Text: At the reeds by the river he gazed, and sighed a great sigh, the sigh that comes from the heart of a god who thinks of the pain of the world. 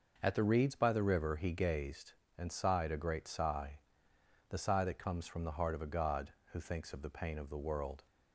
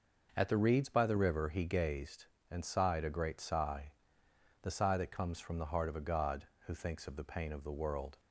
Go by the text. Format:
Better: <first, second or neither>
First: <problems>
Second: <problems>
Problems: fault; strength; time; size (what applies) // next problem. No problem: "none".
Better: neither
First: none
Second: none